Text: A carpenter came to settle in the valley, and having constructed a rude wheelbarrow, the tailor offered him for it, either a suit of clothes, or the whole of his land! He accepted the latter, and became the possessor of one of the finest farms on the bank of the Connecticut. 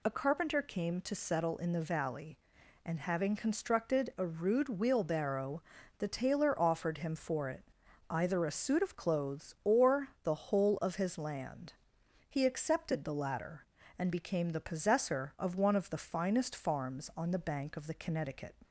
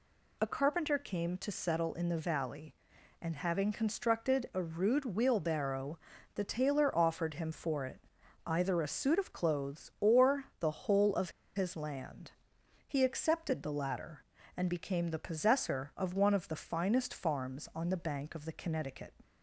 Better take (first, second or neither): first